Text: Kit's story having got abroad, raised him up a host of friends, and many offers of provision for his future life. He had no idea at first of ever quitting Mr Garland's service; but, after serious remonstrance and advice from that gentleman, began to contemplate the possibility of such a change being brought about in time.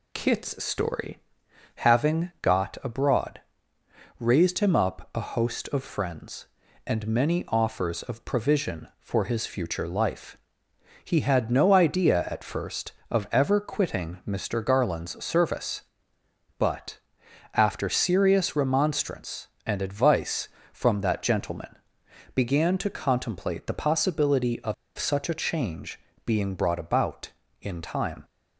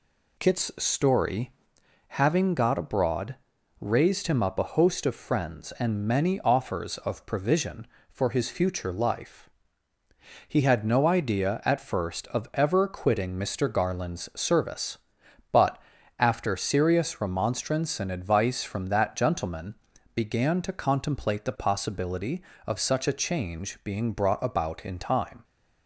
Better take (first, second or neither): second